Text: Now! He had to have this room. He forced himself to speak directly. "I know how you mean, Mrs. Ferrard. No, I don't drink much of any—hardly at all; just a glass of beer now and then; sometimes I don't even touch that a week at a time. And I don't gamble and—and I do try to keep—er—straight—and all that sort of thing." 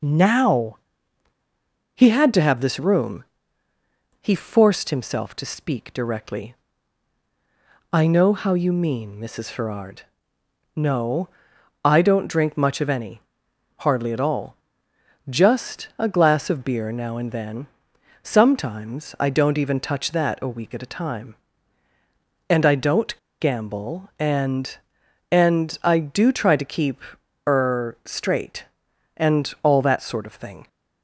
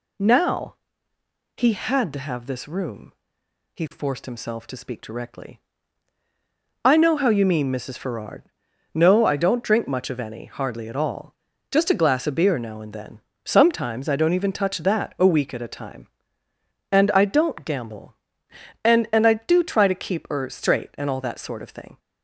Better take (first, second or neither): second